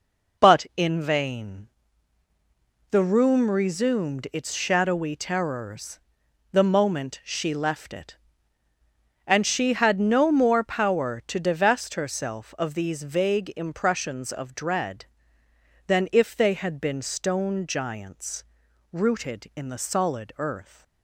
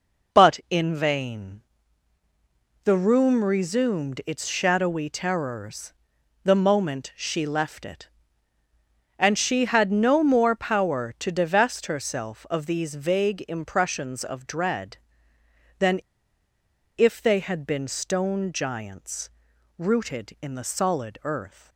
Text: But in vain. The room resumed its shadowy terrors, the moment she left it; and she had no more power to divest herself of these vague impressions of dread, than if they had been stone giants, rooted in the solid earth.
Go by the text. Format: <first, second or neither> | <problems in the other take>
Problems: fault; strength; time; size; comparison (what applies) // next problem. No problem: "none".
first | pauses between "than" and "if"; noticeable; at 15.9 s; 0.97 s long